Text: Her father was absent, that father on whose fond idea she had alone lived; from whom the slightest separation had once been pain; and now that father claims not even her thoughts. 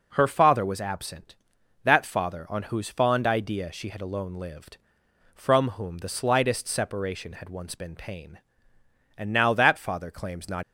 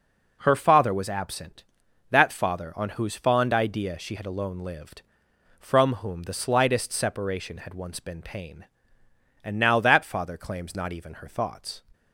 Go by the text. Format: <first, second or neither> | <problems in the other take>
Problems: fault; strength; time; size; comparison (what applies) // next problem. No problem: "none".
second | stops before "even her thoughts"; at 10.6 s